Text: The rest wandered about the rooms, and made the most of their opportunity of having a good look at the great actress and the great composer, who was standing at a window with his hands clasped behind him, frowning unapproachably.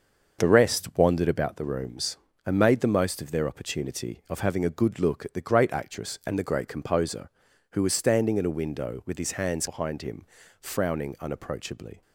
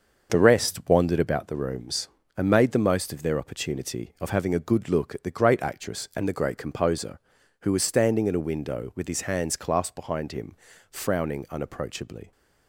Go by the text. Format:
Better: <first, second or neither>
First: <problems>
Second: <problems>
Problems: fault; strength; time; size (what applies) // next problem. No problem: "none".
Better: second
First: starts louder than the rest; until 1.4 s; 6 dB // skips "clasped"; at 9.6 s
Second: starts louder than the rest; until 1.3 s; 6 dB